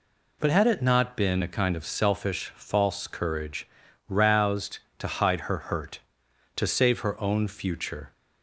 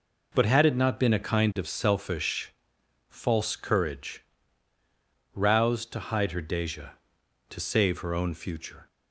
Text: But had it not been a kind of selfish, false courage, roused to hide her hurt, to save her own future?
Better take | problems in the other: first | says "deja" for "hurt"; at 6.4 s

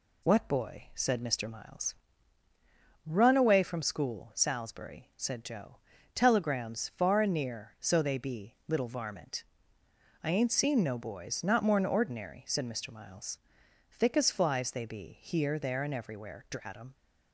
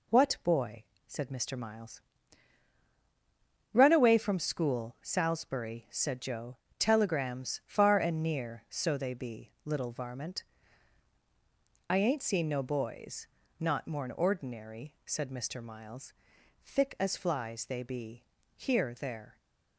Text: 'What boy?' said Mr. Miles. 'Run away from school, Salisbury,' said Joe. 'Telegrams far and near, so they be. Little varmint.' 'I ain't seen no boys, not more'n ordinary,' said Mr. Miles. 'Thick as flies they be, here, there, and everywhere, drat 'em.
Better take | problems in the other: first | stops before "and everywhere drat em"; at 19.3 s

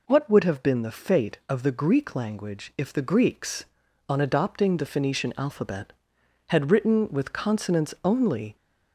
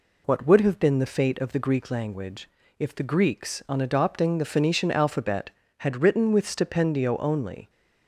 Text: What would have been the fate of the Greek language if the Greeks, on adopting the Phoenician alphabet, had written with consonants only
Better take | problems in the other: first | pauses between "language" and "if"; slight; at 2.4 s; 0.30 s long // says "stipendio" for "consonants"; at 6.4 s

